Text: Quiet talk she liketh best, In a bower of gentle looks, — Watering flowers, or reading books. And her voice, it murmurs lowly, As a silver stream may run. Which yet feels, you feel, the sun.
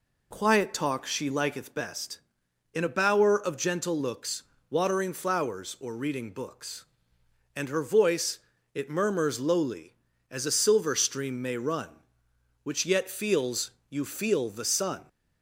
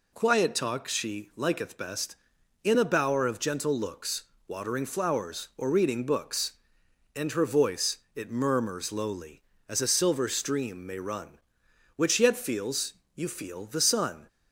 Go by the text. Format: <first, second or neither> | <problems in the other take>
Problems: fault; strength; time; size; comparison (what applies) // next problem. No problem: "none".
neither | none